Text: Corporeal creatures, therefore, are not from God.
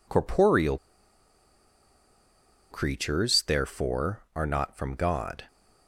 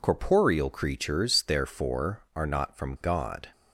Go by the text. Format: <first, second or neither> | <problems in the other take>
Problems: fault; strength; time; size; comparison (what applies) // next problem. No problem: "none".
second | pauses between "Corporeal" and "creatures"; strong; at 0.7 s; 1.9 s long